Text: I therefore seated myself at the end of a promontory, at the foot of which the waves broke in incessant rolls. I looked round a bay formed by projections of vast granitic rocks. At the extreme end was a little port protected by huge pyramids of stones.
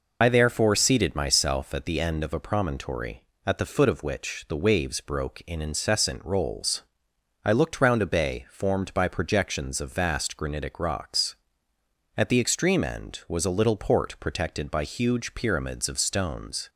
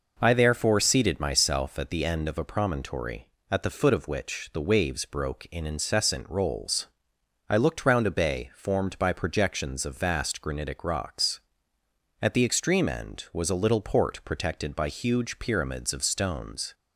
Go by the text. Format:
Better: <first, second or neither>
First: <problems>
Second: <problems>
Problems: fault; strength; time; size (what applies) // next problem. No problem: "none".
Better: second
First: loses the start of "I"; at 0.2 s; 70 ms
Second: none